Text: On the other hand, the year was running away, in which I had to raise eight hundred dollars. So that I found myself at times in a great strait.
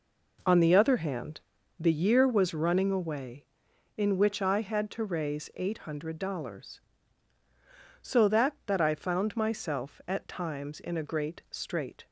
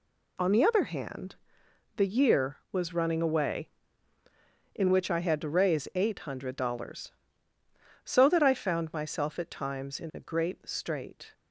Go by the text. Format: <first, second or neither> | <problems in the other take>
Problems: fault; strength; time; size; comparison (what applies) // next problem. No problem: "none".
second | says "that" twice; at 8.6 s